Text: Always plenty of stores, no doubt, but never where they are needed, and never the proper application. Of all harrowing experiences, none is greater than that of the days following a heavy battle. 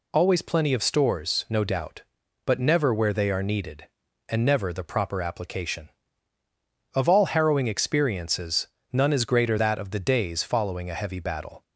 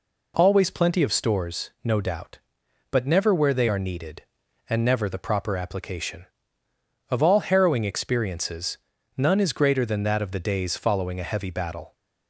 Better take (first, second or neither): second